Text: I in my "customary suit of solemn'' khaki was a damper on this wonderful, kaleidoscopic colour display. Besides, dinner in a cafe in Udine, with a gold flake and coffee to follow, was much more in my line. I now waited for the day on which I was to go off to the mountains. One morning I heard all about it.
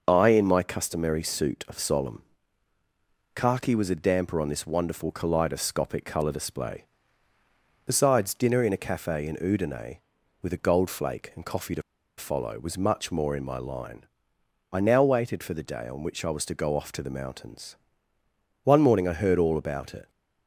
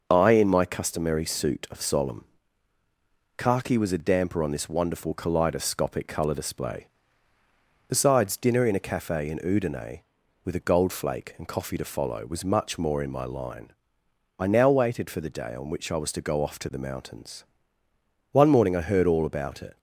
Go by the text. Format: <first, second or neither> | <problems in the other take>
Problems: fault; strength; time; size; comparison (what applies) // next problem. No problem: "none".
second | starts louder than the rest; noticeable; until 1.0 s; 6 dB; noticeable in the second // pauses between "solemn" and "khaki"; at 2.1 s; 1.1 s long; also in the second // pauses between "to" and "follow"; slight; at 11.8 s; 0.35 s long